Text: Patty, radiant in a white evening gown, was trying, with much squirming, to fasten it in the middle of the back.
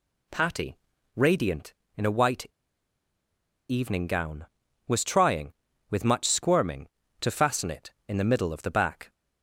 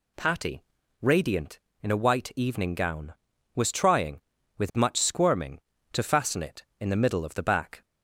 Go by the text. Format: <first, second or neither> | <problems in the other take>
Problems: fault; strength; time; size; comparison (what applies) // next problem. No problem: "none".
second | pauses between "white" and "evening"; at 2.4 s; 1.2 s long